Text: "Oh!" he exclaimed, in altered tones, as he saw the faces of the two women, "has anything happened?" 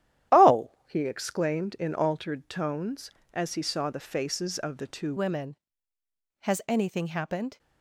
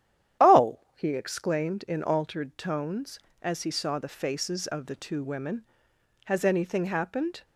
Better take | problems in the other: second | starts louder than the rest; strong; until 1.5 s; 11.5 dB; strong in the second // changes voice at "women"; from 5.1 s on; 2.4 s long

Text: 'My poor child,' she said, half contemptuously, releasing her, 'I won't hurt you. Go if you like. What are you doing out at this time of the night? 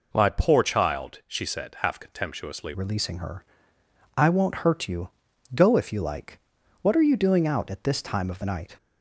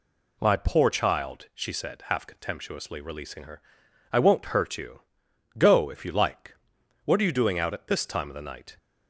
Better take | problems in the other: second | changes voice at "releasing"; from 2.7 s on; 6.0 s long

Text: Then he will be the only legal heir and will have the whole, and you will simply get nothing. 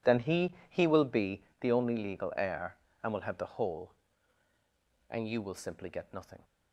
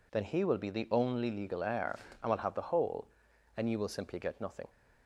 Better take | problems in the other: second | says "he" twice; at 0.7 s // pauses between "be" and "the"; slight; at 1.4 s; 0.18 s long

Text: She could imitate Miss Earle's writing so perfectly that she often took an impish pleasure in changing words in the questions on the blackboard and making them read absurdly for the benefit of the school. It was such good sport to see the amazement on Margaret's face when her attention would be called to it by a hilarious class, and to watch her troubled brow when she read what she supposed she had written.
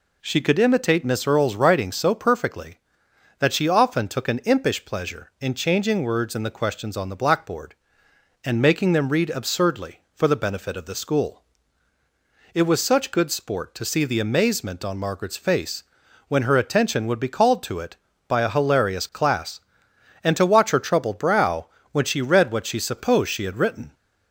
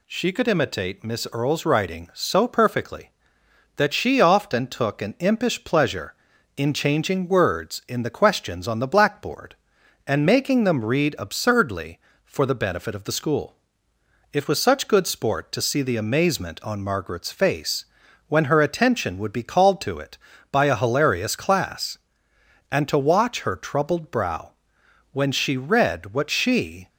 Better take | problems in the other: first | pauses between "face" and "when"; at 17.8 s; 0.42 s long; also in the first // pauses between "brow" and "when"; noticeable; at 24.5 s; 0.60 s long; slight in the first // stops before "supposed she had written"; at 26.8 s

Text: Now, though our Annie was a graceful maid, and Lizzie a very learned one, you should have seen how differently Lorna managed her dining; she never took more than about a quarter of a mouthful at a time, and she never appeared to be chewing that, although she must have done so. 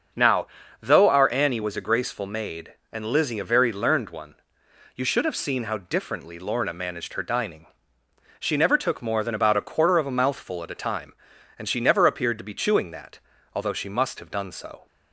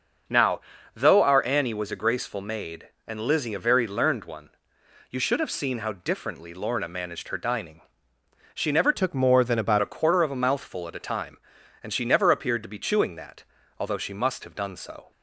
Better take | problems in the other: first | starts louder than the rest; until 1.6 s; 6.5 dB; also in the first // changes voice from "took" to "about"; from 8.9 to 9.7 s; 0.8 s long

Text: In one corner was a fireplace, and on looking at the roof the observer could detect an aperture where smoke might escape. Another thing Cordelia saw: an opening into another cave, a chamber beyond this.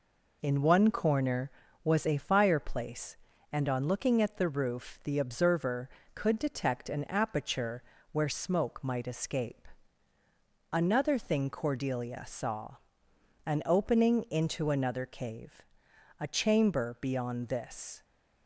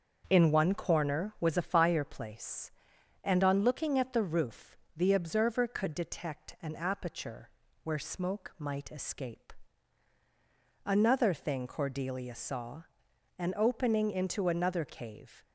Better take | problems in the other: first | starts louder than the rest; until 1.3 s; 6.5 dB // pauses between "roof" and "the"; slight; at 4.7 s; 0.20 s long // pauses between "aperture" and "where"; slight; at 7.4 s; 0.34 s long; slight in the first // stops before "a chamber beyond this"; at 15.4 s

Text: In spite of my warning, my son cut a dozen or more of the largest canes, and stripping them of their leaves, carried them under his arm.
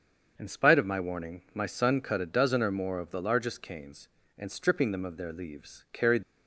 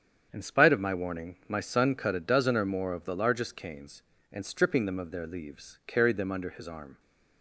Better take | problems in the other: second | starts louder than the rest; until 1.3 s; 7 dB; strong in the second // stops before "them under his arm"; at 6.2 s

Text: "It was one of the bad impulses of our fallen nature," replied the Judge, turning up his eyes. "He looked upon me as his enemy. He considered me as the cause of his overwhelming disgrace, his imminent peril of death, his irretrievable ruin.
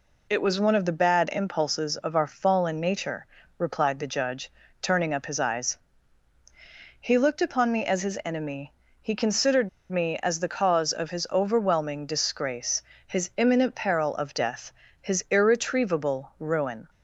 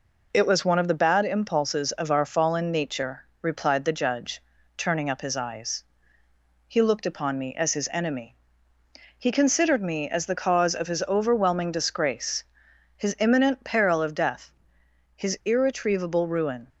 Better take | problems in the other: second | pauses between "considered" and "me"; slight; at 9.6 s; 0.20 s long

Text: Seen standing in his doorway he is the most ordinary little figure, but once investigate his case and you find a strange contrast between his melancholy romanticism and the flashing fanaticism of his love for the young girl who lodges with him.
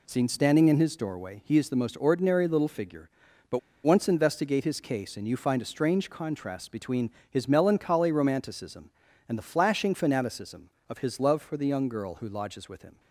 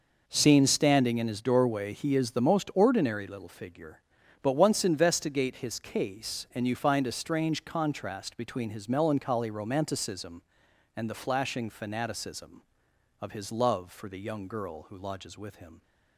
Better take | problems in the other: second | pauses between "but" and "once"; slight; at 3.5 s; 0.25 s long // pauses between "between" and "his"; slight; at 7.0 s; 0.20 s long

